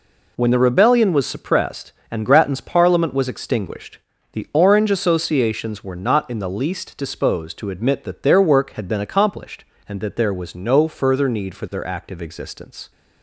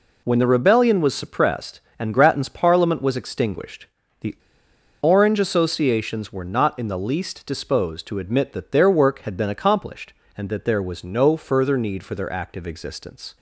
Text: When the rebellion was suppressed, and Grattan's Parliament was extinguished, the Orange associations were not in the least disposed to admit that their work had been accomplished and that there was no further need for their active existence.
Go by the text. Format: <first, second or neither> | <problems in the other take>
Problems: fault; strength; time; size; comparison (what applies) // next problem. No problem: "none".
first | pauses between "the" and "Orange"; noticeable; at 4.3 s; 0.65 s long